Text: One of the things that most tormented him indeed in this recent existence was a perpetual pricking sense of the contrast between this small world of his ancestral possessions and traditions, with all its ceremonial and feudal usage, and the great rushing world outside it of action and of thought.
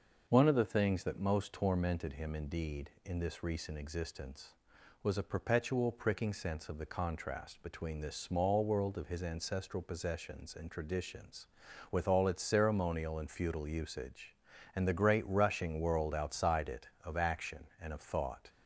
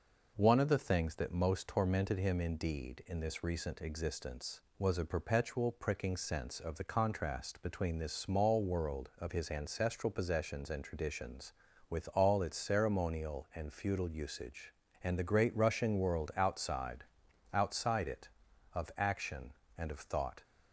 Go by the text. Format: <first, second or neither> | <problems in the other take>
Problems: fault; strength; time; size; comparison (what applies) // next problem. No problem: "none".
first | says "outside" twice; at 17.5 s